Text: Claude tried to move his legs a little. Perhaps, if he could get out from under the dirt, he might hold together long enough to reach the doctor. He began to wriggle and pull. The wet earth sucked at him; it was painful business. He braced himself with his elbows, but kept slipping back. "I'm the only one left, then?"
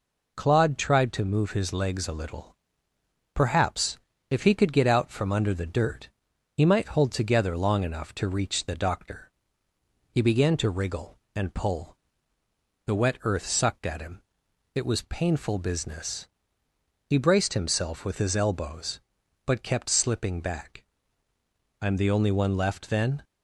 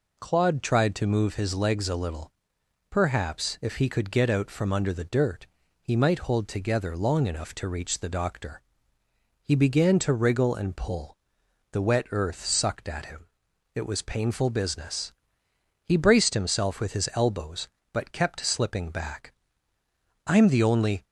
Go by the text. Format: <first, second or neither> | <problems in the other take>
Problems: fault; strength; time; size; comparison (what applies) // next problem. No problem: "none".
first | stops before "one left then"; at 21.0 s